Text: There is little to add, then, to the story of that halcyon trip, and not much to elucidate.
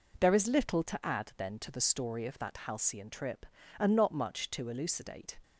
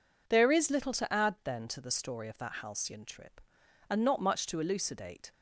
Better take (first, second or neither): neither